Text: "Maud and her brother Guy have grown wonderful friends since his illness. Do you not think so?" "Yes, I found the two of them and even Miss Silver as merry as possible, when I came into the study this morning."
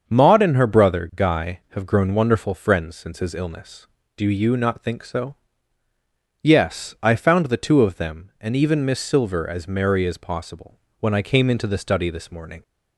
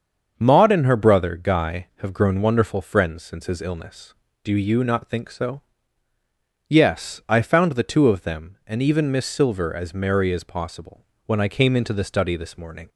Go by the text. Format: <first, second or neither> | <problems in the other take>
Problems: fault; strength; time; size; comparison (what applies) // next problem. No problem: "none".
neither | starts louder than the rest; the same in both